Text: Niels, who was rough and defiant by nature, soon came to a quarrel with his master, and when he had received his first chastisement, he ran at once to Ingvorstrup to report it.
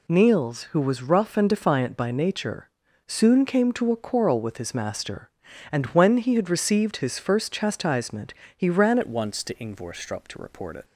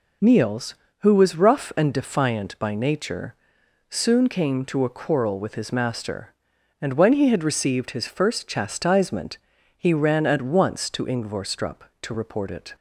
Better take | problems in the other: second | changes voice at "at"; from 9.0 s on; 1.8 s long

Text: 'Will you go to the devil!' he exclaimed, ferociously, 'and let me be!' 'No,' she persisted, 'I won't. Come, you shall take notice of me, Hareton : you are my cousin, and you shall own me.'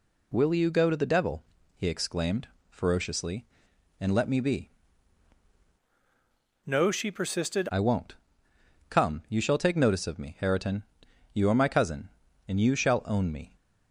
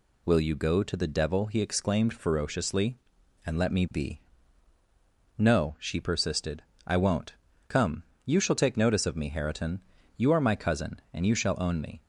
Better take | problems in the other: second | changes voice from "No" to "persisted"; from 6.6 to 7.6 s; 1.0 s long

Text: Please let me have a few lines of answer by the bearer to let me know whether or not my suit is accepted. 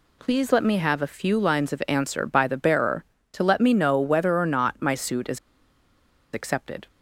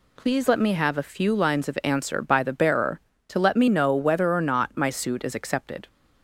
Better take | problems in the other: second | pauses between "is" and "accepted"; noticeable; at 5.3 s; 0.95 s long

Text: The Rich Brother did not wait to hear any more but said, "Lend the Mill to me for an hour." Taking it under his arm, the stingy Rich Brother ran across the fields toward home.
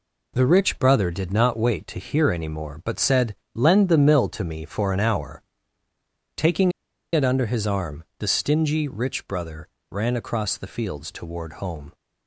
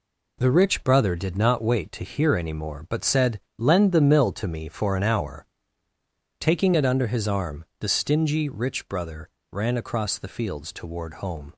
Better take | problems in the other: second | pauses between "Taking" and "it"; at 6.7 s; 0.42 s long // pauses between "Brother" and "ran"; slight; at 9.6 s; 0.22 s long; slight in the second

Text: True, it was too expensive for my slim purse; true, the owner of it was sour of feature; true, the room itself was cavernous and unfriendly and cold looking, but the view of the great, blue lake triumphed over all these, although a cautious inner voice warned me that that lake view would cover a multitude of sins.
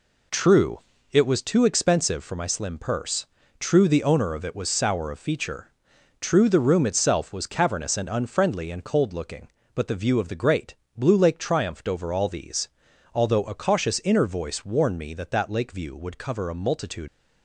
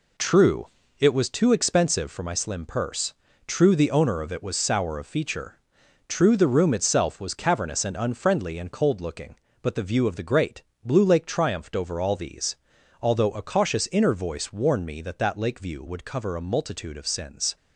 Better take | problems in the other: second | stops before "of sins"; at 17.0 s

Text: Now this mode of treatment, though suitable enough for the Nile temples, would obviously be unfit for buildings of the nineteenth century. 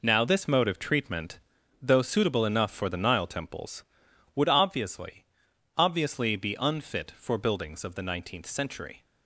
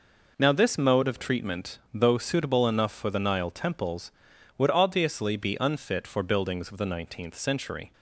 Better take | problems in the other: second | says "obviously" twice; at 5.7 s

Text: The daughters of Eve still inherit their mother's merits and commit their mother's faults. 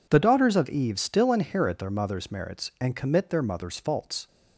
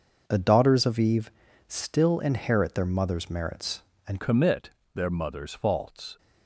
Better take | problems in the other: first | pauses between "Eve" and "still"; at 1.2 s; 0.38 s long // changes voice at "commit"; from 4.1 s on; 2.0 s long // pauses between "commit" and "their"; slight; at 4.7 s; 0.24 s long

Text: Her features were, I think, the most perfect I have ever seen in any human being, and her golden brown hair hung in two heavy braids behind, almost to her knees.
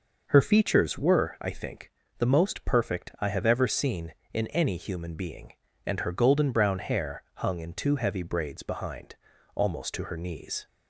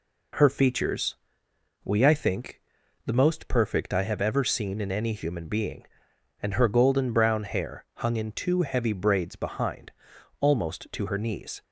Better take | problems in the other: first | says "we" for "were"; at 1.8 s

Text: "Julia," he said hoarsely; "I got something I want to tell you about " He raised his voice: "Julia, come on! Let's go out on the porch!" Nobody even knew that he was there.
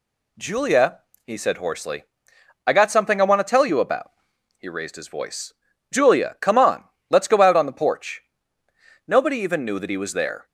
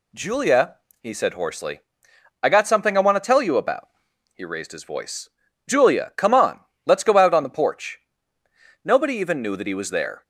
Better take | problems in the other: neither | none

